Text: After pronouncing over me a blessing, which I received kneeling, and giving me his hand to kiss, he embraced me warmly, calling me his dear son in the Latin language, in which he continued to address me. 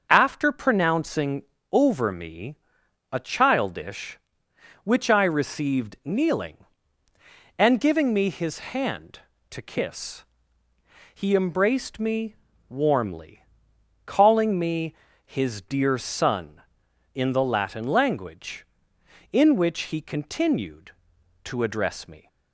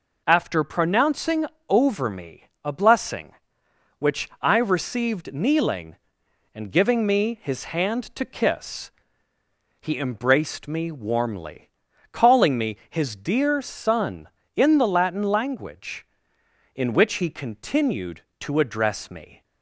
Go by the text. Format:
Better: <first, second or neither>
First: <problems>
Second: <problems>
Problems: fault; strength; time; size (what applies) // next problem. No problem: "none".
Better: second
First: starts louder than the rest; until 1.1 s; 6.5 dB // pauses between "pronouncing" and "over"; slight; at 1.4 s; 0.28 s long // pauses between "me" and "a"; noticeable; at 2.5 s; 0.56 s long // says "childish" for "blessing"; at 3.1 s // pauses between "me" and "warmly"; slight; at 12.3 s; 0.34 s long // pauses between "me" and "his"; slight; at 14.9 s; 0.30 s long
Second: pauses between "pronouncing" and "over"; slight; at 1.4 s; 0.24 s long // pauses between "me" and "a"; slight; at 2.4 s; 0.18 s long